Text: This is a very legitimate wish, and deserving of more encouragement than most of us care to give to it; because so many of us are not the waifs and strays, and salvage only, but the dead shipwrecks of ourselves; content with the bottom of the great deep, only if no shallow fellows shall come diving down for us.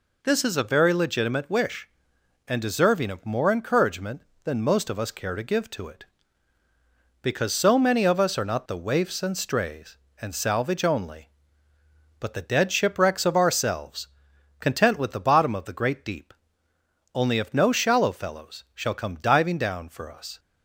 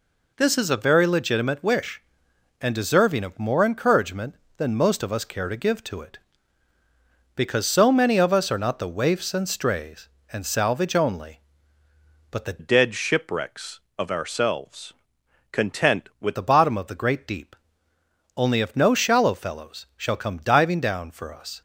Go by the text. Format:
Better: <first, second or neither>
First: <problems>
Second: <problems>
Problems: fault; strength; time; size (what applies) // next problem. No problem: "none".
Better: first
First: none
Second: changes voice from "dead" to "with"; from 12.5 to 16.3 s; 3.8 s long